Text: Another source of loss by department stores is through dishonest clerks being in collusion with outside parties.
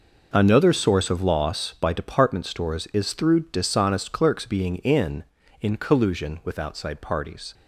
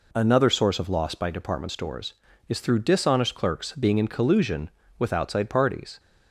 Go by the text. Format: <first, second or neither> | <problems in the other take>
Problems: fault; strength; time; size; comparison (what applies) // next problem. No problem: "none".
second | says "in" twice; at 5.5 s